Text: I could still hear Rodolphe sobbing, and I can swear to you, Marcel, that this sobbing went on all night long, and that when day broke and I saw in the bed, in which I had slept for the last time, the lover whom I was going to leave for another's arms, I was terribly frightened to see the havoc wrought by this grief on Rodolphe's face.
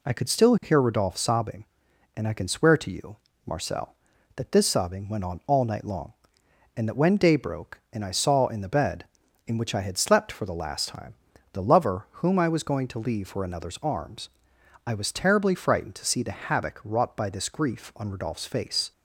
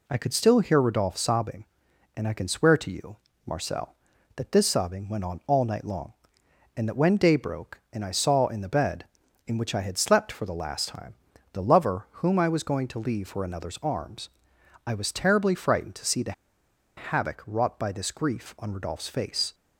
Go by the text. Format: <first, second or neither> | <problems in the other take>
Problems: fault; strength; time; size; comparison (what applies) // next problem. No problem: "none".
first | pauses between "the" and "havoc"; noticeable; at 16.3 s; 0.65 s long